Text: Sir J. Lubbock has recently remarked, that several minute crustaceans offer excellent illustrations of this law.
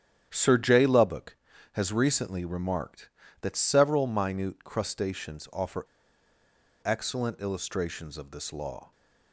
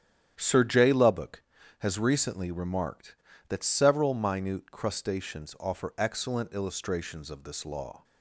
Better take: second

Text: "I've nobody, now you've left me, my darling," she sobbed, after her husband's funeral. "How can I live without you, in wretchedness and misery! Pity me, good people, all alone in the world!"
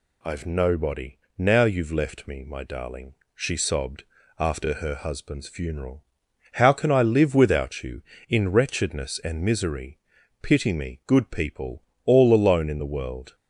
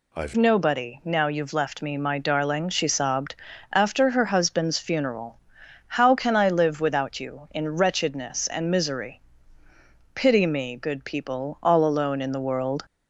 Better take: first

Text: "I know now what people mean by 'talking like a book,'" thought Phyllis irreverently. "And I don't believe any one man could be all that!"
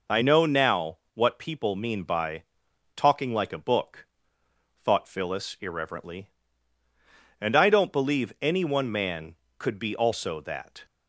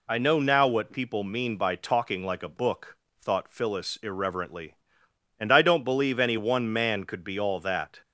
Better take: second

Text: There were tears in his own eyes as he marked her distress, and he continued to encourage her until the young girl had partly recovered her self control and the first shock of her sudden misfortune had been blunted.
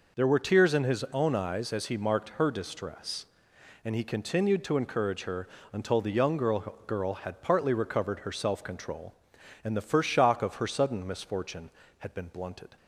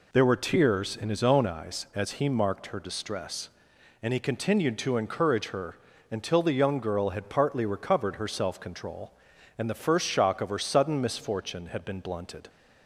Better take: second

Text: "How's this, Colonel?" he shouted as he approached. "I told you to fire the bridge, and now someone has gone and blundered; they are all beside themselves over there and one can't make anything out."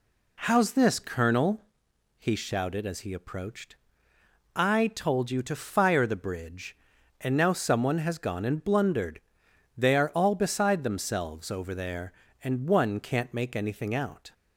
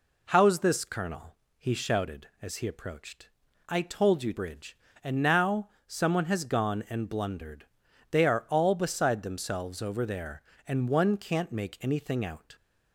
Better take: first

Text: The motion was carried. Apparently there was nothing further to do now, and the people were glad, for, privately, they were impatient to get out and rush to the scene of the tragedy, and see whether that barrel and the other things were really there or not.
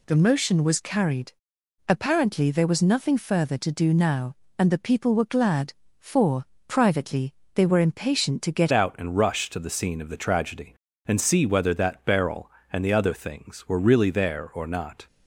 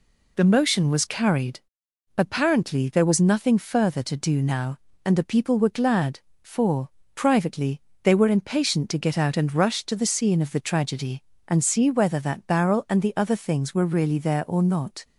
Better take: second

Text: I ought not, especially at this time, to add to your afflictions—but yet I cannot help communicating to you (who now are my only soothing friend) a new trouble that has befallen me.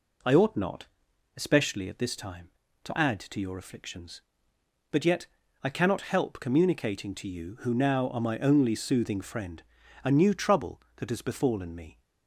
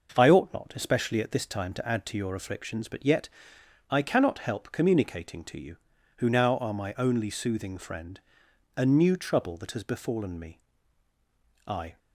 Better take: first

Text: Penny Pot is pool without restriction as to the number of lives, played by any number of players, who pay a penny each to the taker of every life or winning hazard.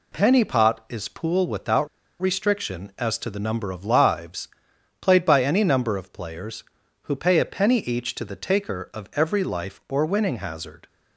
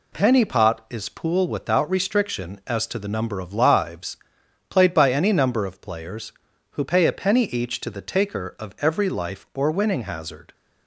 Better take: second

